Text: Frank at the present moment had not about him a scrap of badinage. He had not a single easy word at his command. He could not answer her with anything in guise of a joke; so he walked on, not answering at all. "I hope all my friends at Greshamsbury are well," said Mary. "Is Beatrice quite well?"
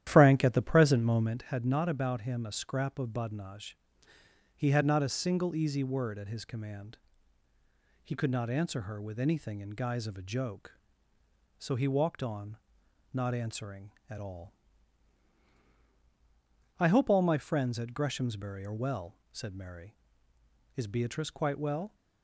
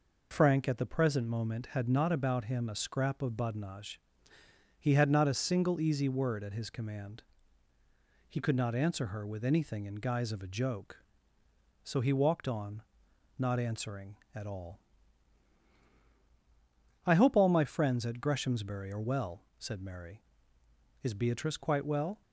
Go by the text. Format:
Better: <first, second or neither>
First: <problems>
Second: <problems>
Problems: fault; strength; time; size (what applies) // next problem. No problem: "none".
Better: second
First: starts louder than the rest; strong; until 1.5 s; 11.5 dB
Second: none